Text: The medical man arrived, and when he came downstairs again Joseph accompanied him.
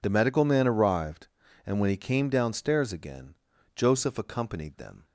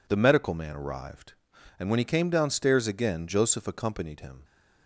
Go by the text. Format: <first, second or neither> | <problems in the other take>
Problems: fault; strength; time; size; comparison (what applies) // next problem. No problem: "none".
second | pauses between "again" and "Joseph"; at 3.3 s; 0.40 s long // says "them" for "him"; at 4.7 s